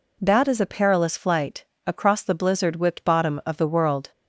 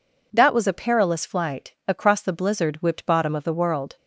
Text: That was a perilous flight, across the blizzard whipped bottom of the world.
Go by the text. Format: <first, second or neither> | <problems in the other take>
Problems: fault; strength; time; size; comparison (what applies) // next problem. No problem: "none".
second | says "is" for "was"; at 0.4 s